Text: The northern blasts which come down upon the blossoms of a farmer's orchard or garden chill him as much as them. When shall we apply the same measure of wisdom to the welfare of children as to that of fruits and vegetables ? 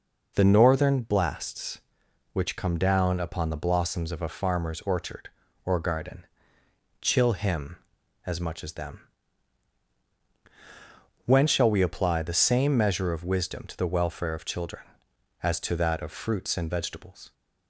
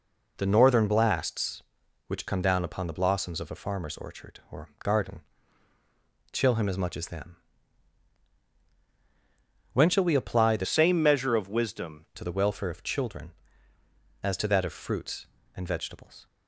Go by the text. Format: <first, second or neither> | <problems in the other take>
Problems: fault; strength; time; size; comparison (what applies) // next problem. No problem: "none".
first | pauses between "garden" and "chill"; at 5.2 s; 1.1 s long; noticeable in the first // changes voice from "same" to "wisdom"; from 10.6 to 12.0 s; 1.4 s long